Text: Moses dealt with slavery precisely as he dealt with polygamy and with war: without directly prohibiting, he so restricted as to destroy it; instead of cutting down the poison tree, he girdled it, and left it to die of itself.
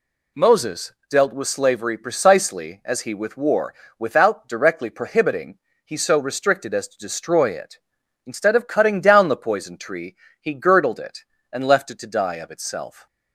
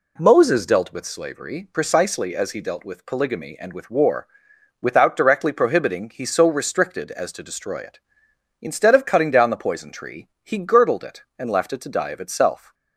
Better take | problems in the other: second | pauses between "Moses" and "dealt"; slight; at 0.9 s; 0.18 s long // skips "dealt with polygamy and"; at 3.1 s

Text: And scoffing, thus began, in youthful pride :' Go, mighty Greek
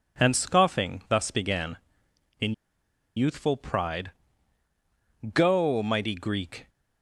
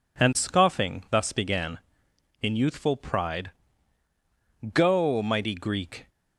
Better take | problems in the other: second | pauses between "in" and "youthful"; noticeable; at 2.5 s; 0.62 s long

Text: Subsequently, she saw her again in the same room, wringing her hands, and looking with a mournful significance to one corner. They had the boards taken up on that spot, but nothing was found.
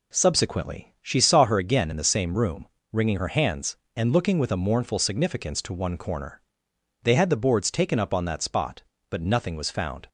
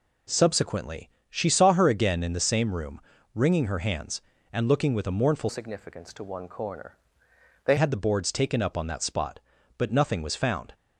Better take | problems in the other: first | changes voice from "significance" to "They"; from 5.4 to 7.7 s; 2.3 s long

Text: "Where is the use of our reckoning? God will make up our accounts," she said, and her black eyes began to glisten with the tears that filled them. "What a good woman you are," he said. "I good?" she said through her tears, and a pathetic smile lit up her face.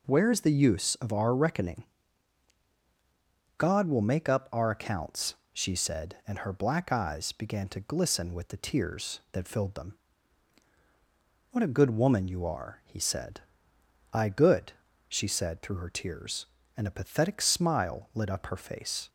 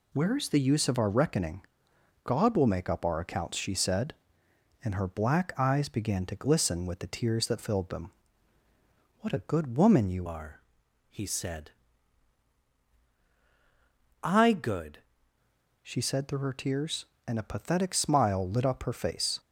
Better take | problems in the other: first | changes voice from "are" to "good"; from 10.2 to 14.9 s; 4.7 s long

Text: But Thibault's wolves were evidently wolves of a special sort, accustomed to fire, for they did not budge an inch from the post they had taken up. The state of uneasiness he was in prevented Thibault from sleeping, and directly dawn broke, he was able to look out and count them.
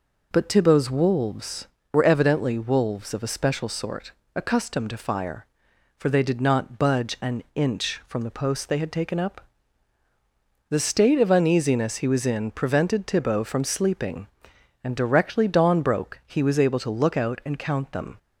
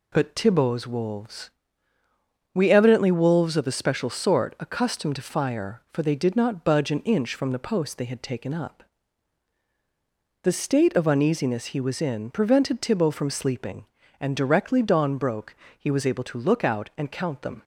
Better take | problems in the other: first | says "we" for "were"; at 2.5 s

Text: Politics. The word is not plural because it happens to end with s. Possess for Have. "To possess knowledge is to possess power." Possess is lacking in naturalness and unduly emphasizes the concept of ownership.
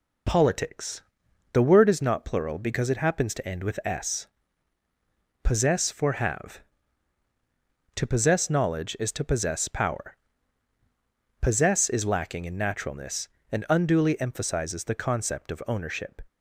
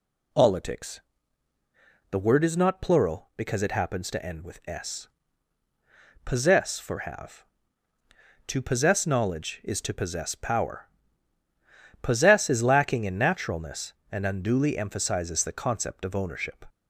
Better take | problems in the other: neither | none

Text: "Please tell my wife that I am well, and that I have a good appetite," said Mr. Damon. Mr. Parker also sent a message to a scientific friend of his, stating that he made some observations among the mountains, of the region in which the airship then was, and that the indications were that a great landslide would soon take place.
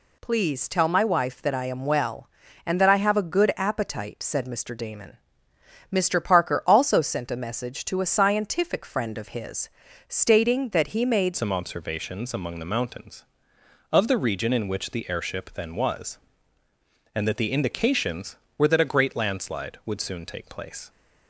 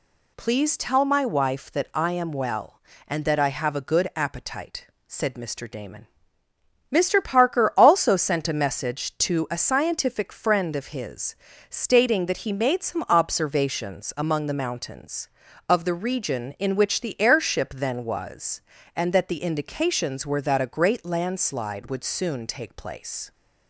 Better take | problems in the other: second | changes voice at "some"; from 11.3 s on; 9.5 s long

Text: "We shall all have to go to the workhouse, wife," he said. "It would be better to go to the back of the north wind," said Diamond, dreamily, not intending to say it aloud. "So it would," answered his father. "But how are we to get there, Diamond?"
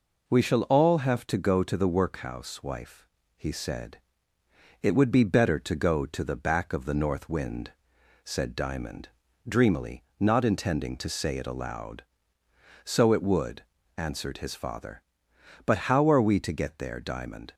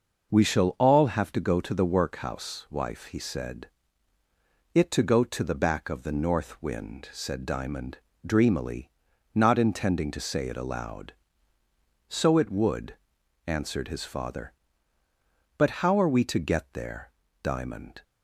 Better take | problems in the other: first | skips "would be better"; at 4.9 s

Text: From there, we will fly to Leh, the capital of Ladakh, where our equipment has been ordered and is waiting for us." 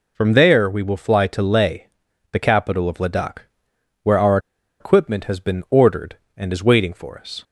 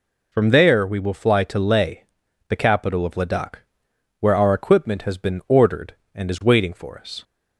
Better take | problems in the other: second | pauses between "our" and "equipment"; at 4.3 s; 0.42 s long

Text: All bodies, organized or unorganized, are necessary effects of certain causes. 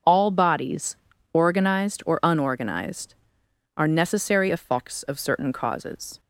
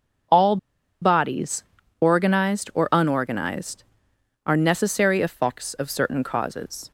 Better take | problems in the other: first | starts louder than the rest; until 2.1 s; 6.5 dB; also in the first // pauses between "All" and "bodies"; at 0.5 s; 0.45 s long

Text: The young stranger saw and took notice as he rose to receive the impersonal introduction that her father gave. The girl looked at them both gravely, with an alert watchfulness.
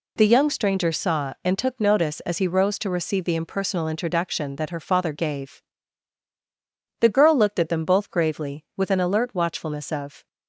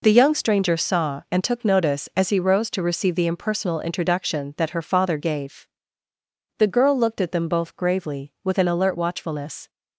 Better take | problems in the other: second | goes on to say "Of"; slight; from 9.9 s on; 0.36 s long

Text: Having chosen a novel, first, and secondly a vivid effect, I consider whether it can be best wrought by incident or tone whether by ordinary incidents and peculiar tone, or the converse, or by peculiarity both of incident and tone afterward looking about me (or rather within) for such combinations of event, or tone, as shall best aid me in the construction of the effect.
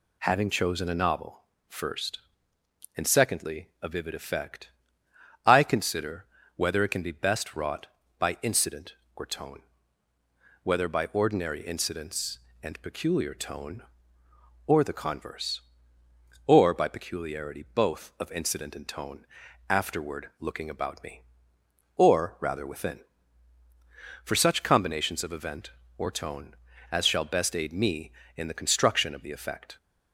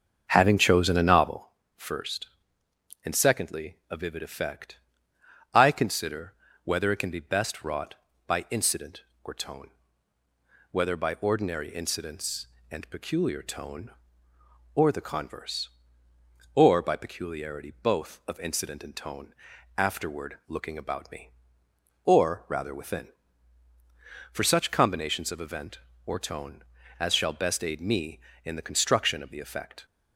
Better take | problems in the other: first | starts louder than the rest; until 1.5 s; 7 dB // pauses between "consider" and "whether"; slight; at 6.3 s; 0.30 s long; slight in the first // pauses between "tone" and "whether"; at 9.6 s; 1.0 s long; also in the first // pauses between "tone" and "afterward"; at 19.3 s; 0.44 s long; also in the first

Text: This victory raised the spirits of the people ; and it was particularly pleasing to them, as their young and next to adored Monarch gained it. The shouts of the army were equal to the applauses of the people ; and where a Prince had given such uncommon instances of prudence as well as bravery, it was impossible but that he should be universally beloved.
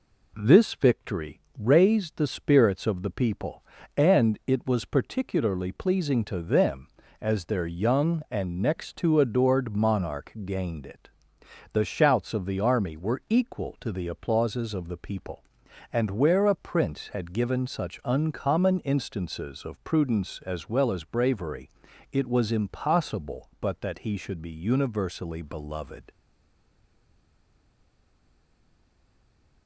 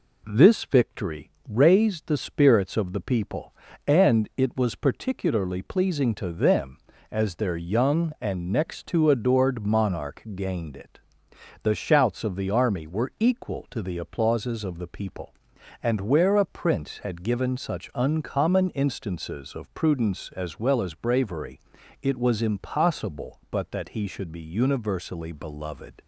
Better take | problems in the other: second | pauses between "victory" and "raised"; slight; at 1.3 s; 0.18 s long; slight in the second // stays silent after the last word; strong; from 26.1 s on; 3.5 s long

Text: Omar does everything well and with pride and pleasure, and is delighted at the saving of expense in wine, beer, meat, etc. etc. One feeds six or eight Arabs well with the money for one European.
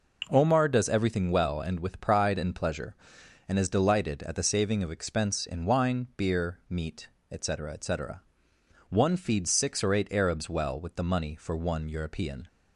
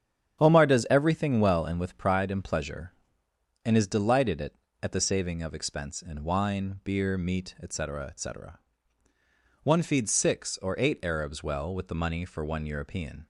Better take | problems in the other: first | starts louder than the rest; strong; until 1.4 s; 8.5 dB // says "at" twice; at 4.8 s

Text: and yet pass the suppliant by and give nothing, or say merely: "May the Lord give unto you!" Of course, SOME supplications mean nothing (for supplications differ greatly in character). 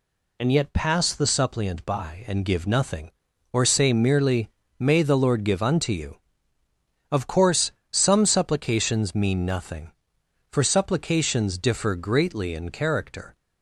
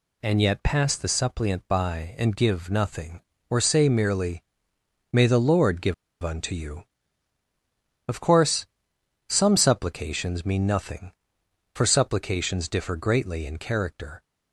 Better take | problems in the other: first | pauses between "give" and "unto"; slight; at 5.9 s; 0.28 s long

